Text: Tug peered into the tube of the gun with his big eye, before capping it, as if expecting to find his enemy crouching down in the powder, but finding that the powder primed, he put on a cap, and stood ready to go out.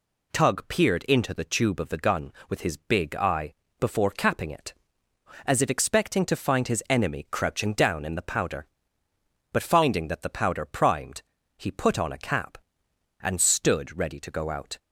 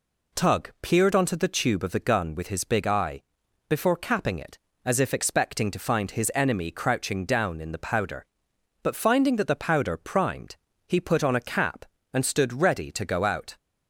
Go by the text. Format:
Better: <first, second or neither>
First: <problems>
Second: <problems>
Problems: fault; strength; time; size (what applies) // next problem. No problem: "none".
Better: first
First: none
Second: says "onto" for "into"; at 1.1 s